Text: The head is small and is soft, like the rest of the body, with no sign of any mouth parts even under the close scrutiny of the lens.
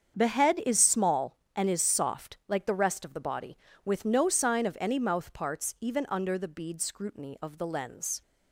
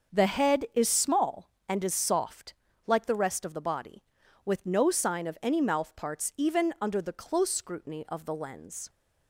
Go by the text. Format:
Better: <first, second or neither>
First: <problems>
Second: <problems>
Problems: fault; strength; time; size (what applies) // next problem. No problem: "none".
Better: second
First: starts louder than the rest; strong; until 1.2 s; 7.5 dB // says "bead" for "close"; at 6.4 s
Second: starts louder than the rest; until 1.2 s; 6.5 dB